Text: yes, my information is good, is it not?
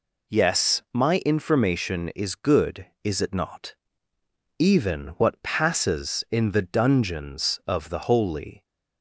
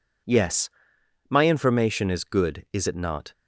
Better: second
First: goes on to say "Even what passes in the dungeons of the Holy"; strong; from 4.5 s on; 4.0 s long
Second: none

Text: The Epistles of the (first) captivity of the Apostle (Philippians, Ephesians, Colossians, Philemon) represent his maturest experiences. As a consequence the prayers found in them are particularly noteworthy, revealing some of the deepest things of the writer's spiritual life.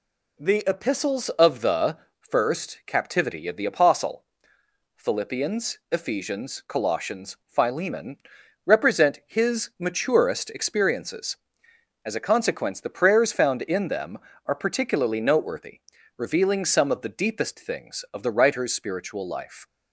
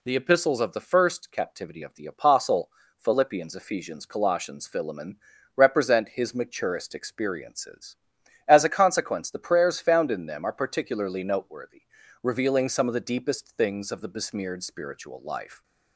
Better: first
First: none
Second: says "besmeared" for "writer's"; at 14.0 s

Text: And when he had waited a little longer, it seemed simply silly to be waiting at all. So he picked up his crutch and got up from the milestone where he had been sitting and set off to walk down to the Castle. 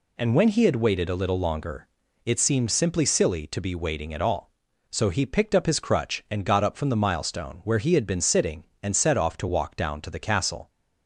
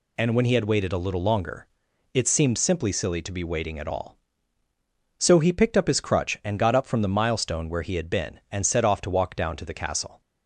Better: first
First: none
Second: skips "sitting"; at 8.4 s

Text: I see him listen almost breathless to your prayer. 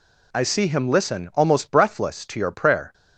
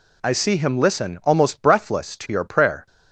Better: neither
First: none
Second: none

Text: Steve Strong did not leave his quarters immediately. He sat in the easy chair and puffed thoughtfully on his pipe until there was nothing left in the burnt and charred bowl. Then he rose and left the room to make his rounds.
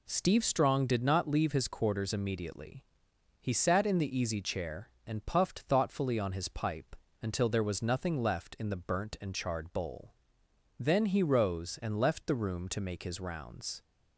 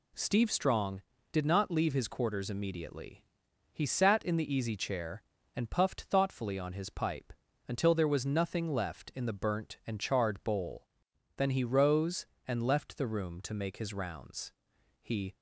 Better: first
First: pauses between "pipe" and "until"; slight; at 6.9 s; 0.26 s long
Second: pauses between "pipe" and "until"; slight; at 7.3 s; 0.34 s long // goes on to say "He"; slight; from 15.0 s on; 0.32 s long

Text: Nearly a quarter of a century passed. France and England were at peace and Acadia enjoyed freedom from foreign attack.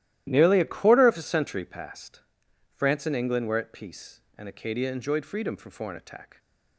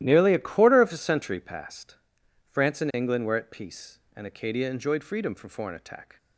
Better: neither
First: starts louder than the rest; strong; until 1.2 s; 13.5 dB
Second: starts louder than the rest; strong; until 1.0 s; 13.5 dB

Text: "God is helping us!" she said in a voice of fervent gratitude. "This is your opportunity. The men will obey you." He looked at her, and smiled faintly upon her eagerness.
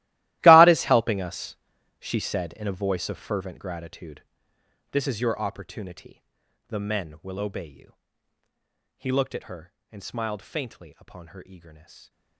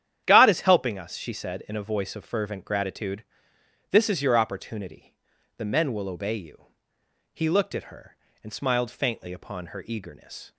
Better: second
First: gets quieter; strong; throughout; 18.5 dB // starts louder than the rest; strong; until 1.4 s; 16.5 dB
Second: starts louder than the rest; strong; until 1.2 s; 10.5 dB

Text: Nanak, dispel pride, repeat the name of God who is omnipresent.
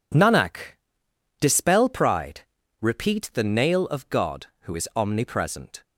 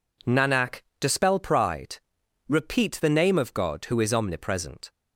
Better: second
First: says "nail" for "name"; at 3.4 s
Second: none

